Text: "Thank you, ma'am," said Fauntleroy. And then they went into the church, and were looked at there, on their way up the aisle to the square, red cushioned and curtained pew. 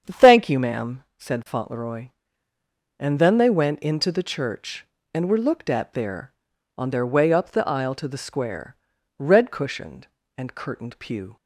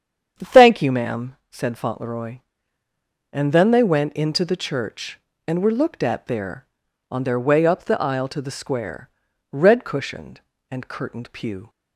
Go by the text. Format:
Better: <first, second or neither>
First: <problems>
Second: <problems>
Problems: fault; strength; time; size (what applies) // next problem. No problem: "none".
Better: neither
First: starts louder than the rest; strong; until 1.2 s; 8 dB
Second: starts louder than the rest; strong; until 1.5 s; 8 dB